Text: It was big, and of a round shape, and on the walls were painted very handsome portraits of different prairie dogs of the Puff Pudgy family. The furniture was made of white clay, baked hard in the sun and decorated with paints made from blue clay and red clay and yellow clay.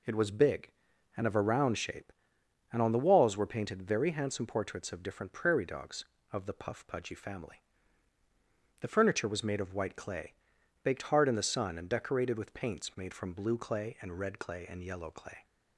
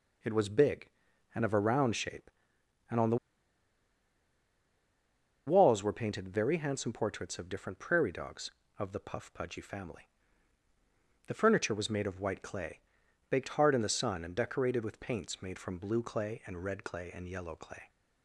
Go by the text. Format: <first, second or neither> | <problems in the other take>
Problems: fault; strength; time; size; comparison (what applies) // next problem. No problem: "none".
first | pauses between "the" and "walls"; strong; at 3.1 s; 2.2 s long